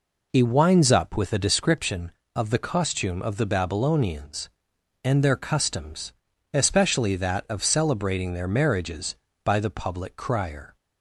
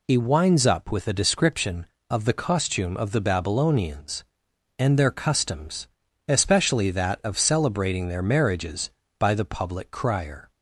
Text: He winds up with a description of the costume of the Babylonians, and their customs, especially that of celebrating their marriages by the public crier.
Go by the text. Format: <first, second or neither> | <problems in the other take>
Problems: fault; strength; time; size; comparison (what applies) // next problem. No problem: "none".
second | starts louder than the rest; noticeable; until 1.6 s; 4 dB